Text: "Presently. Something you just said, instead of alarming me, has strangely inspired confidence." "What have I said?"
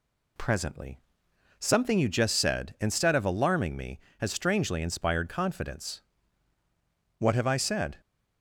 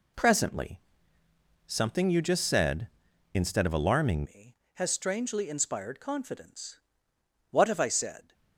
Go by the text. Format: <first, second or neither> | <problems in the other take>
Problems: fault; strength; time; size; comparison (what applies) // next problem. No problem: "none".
first | changes voice at "me"; from 4.2 s on; 4.1 s long